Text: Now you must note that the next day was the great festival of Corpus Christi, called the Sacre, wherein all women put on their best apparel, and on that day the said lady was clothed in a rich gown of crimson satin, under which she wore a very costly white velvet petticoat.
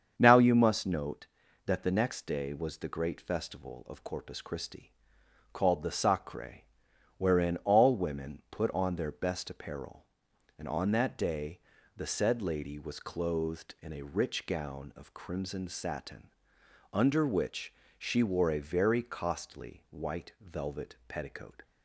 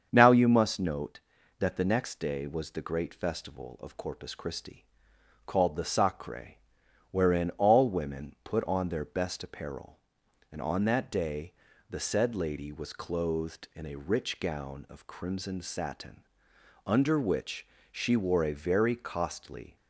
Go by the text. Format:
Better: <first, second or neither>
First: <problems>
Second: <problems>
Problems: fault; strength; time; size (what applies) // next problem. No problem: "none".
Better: first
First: starts louder than the rest; strong; until 1.1 s; 7.5 dB // pauses between "day" and "the"; at 11.5 s; 0.38 s long // pauses between "which" and "she"; slight; at 17.7 s; 0.26 s long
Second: starts louder than the rest; strong; until 1.1 s; 7.5 dB // pauses between "day" and "the"; at 11.5 s; 0.38 s long // pauses between "which" and "she"; slight; at 17.6 s; 0.26 s long // stops before "white velvet petticoat"; at 19.7 s